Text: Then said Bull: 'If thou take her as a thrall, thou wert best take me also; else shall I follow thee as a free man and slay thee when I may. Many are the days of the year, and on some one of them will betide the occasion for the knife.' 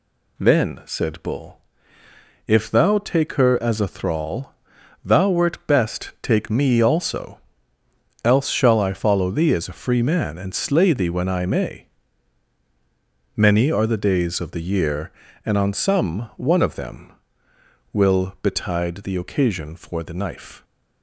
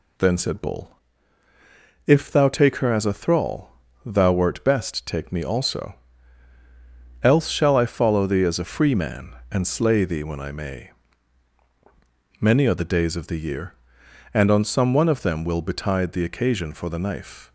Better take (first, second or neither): neither